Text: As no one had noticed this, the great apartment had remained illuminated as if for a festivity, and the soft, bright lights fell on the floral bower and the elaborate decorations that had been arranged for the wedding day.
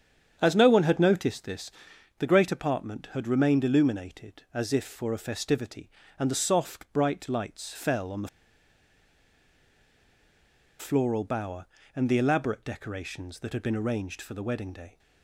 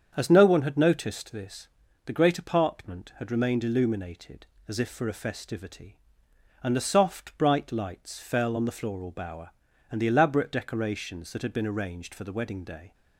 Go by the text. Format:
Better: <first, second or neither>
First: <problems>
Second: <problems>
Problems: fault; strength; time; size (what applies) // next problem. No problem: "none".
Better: second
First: starts louder than the rest; strong; until 1.4 s; 8 dB // pauses between "the" and "floral"; strong; at 8.2 s; 2.5 s long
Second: starts louder than the rest; strong; until 1.1 s; 7.5 dB